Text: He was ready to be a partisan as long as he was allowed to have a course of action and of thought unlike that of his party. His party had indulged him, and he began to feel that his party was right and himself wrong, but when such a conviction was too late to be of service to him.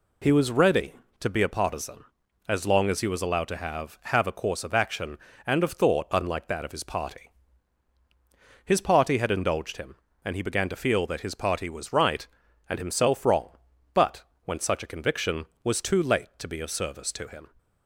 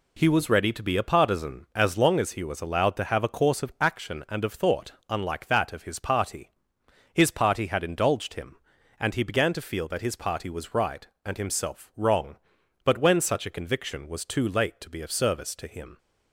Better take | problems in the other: second | says "have" twice; at 4.0 s // pauses between "but" and "when"; slight; at 14.2 s; 0.22 s long

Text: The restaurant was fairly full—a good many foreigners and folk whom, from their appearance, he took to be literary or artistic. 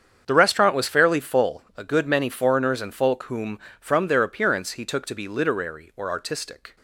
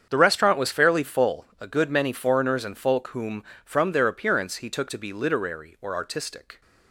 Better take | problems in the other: neither | starts louder than the rest; strong; the same in both

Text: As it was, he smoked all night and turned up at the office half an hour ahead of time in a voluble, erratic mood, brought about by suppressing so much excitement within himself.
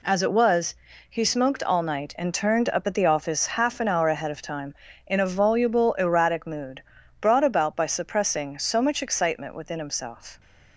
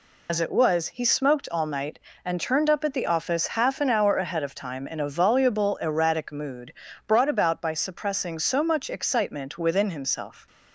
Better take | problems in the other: first | loses the start of "As"; at 0.2 s; 75 ms

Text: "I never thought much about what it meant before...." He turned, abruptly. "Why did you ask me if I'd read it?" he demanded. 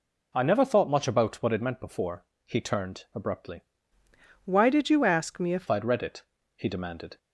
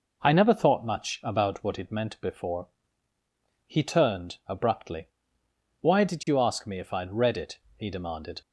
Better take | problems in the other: second | changes voice from "Why" to "if"; from 4.4 to 5.6 s; 1.2 s long

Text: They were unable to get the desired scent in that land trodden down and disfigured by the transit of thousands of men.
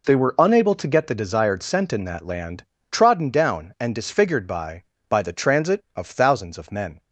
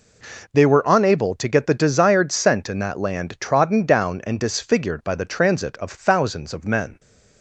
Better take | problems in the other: second | pauses between "land" and "trodden"; slight; at 2.6 s; 0.28 s long // says "by" twice; at 5.0 s

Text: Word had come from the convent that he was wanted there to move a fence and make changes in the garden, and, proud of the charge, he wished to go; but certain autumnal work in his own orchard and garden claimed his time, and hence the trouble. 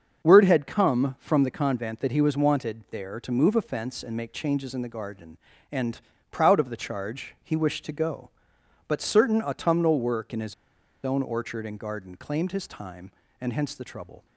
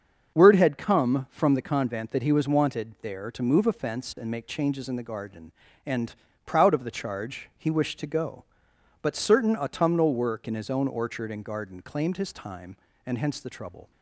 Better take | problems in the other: second | starts louder than the rest; until 1.3 s; 6.5 dB; also in the second // pauses between "his" and "own"; noticeable; at 10.5 s; 0.50 s long

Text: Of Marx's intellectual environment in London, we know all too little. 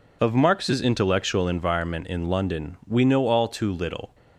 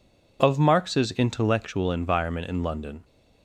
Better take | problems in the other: first | stops before "we know all too little"; at 3.0 s

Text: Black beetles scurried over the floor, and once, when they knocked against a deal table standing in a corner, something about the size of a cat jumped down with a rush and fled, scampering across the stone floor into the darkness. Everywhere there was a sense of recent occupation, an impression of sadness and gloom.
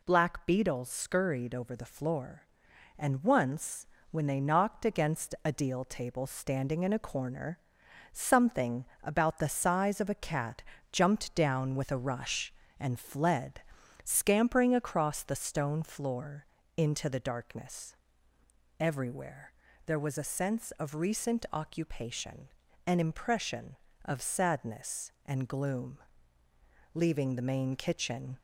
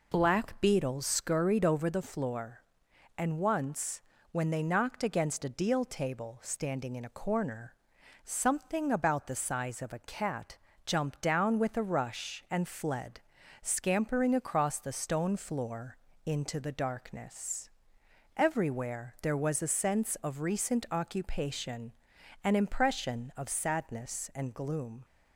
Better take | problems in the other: second | pauses between "something" and "about"; slight; at 8.8 s; 0.20 s long // pauses between "cat" and "jumped"; slight; at 10.6 s; 0.26 s long; slight in the second // pauses between "floor" and "into"; slight; at 16.4 s; 0.30 s long; slight in the second // pauses between "Everywhere" and "there"; slight; at 19.5 s; 0.34 s long // goes on to say "Leaving the main kitchen"; from 26.9 s on; 1.4 s long

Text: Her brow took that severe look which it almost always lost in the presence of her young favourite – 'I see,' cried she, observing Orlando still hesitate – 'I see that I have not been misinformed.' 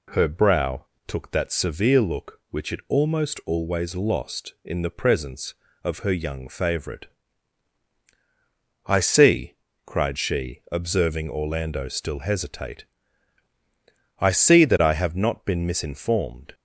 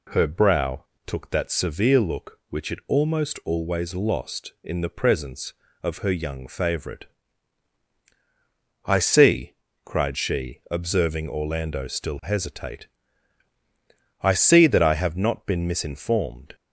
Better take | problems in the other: neither | pauses between "brow" and "took"; slight; the same in both

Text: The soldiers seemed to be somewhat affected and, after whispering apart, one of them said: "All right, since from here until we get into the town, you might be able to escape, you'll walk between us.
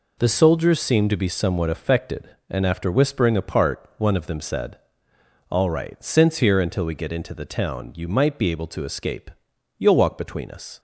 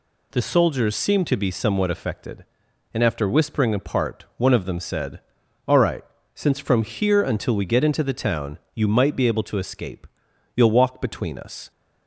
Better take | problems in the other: second | skips "from"; at 6.3 s

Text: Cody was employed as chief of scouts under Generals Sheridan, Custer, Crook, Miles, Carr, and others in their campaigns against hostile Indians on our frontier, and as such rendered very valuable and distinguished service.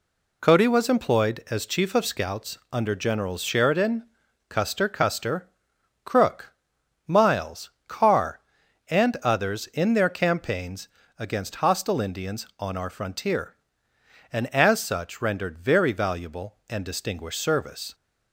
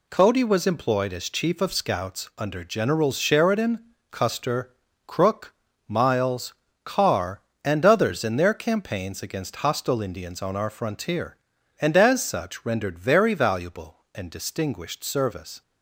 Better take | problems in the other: second | pauses between "scouts" and "under"; slight; at 2.5 s; 0.16 s long // says "Custer" twice; at 4.8 s // pauses between "campaigns" and "against"; slight; at 10.8 s; 0.30 s long

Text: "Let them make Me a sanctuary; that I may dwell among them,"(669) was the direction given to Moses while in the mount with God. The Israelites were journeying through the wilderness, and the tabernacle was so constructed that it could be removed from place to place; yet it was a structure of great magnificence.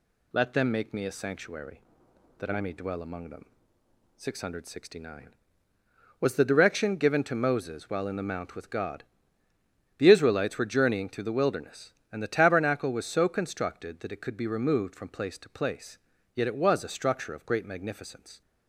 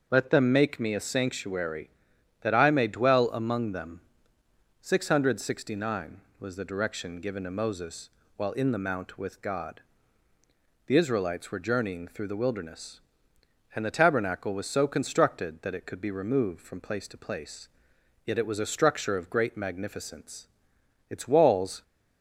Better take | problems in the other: first | starts louder than the rest; strong; until 1.1 s; 7 dB // pauses between "Moses" and "while"; slight; at 8.0 s; 0.28 s long // goes on to say "Its walls"; noticeable; from 21.1 s on; 0.72 s long

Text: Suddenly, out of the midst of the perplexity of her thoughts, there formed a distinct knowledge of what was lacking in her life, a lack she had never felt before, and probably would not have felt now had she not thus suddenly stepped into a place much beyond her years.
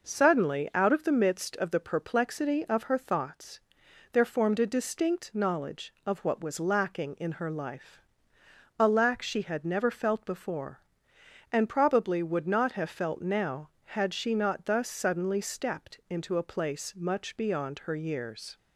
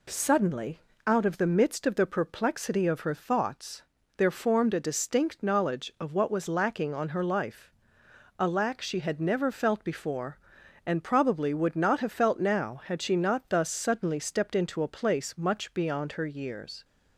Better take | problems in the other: first | says "on" for "in"; at 6.9 s

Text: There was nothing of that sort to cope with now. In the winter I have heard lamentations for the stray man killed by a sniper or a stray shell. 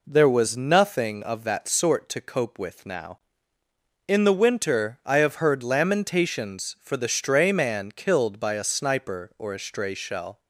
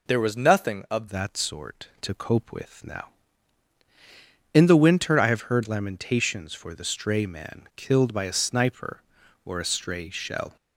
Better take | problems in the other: first | changes voice at "that"; from 1.0 s on; 9.5 s long

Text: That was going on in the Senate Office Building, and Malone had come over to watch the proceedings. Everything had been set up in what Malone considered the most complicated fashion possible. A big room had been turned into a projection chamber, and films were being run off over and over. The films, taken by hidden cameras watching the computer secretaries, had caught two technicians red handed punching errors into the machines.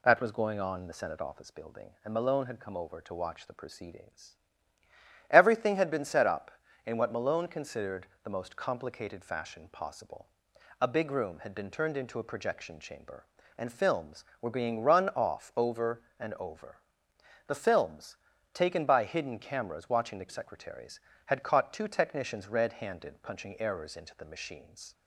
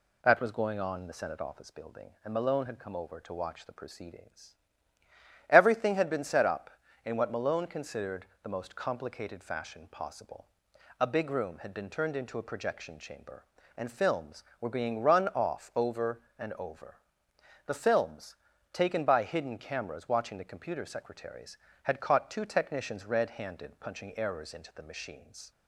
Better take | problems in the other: second | pauses between "considered" and "the"; slight; at 8.0 s; 0.16 s long; slight in the second // skips "computer"; at 20.2 s

